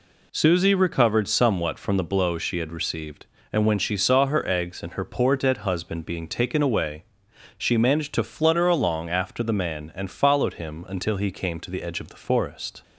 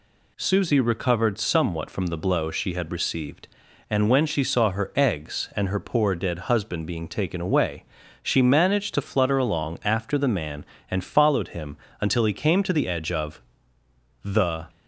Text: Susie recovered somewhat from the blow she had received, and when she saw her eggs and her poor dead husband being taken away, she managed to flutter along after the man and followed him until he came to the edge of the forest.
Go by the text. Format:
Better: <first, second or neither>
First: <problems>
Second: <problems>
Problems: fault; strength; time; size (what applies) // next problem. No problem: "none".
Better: first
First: none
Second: pauses between "him" and "until"; slight; at 11.7 s; 0.24 s long // pauses between "of" and "the"; noticeable; at 13.4 s; 0.82 s long // stops before "forest"; at 14.6 s